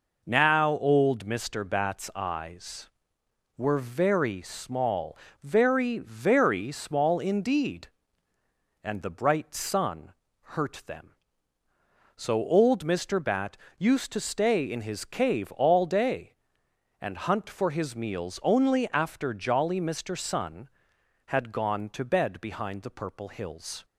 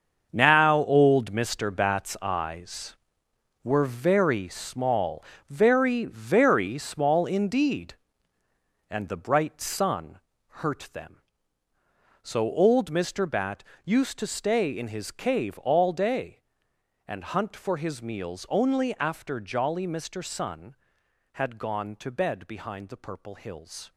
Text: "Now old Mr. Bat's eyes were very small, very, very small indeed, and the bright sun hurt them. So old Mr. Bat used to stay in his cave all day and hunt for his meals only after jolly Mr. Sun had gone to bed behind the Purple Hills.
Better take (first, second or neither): first